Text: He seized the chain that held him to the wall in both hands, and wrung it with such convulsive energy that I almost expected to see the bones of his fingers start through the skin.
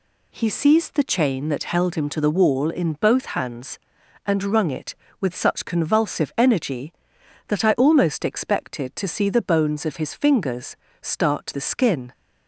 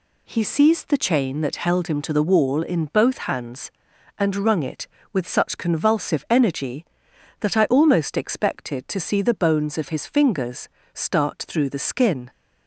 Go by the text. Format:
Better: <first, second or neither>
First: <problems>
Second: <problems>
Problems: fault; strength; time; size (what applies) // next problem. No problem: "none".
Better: second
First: pauses between "fingers" and "start"; slight; at 10.7 s; 0.24 s long // skips "through"; at 11.5 s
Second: pauses between "fingers" and "start"; slight; at 10.6 s; 0.24 s long